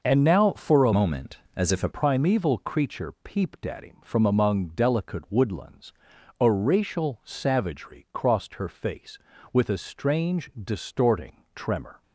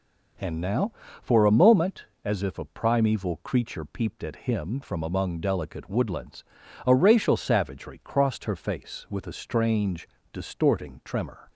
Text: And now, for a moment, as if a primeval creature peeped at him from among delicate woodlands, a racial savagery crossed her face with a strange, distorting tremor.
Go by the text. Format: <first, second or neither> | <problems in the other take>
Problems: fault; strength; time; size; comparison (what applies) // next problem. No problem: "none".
second | changes voice from "moment" to "a"; from 0.9 to 1.8 s; 0.9 s long